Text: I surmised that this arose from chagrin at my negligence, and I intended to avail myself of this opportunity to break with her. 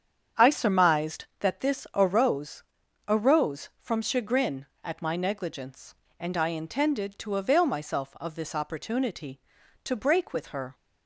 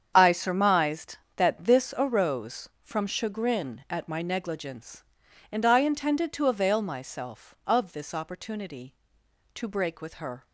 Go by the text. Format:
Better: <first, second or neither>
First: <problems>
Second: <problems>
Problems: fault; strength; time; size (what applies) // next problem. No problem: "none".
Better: second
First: starts louder than the rest; strong; until 1.5 s; 8 dB // says "arose" twice; at 3.0 s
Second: starts louder than the rest; strong; until 1.1 s; 7.5 dB